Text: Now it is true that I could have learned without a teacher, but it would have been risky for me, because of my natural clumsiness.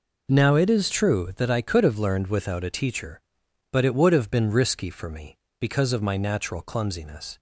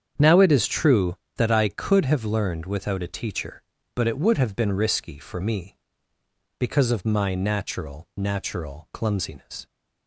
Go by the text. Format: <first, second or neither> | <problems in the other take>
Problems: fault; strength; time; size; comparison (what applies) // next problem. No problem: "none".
first | starts louder than the rest; strong; until 1.3 s; 8 dB // says "natural" twice; at 8.1 s